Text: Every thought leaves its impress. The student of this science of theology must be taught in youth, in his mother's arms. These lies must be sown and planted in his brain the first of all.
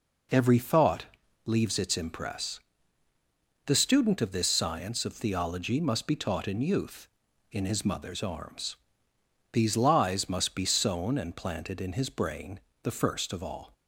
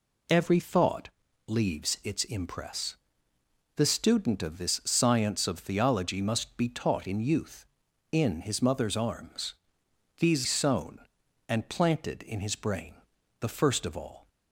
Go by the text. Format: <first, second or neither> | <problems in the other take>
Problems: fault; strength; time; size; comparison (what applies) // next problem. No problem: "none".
first | pauses between "thought" and "leaves"; at 1.0 s; 0.38 s long; also in the first // skips "lies must be"; at 10.4 s // pauses between "brain" and "the"; noticeable; at 12.9 s; 0.46 s long; slight in the first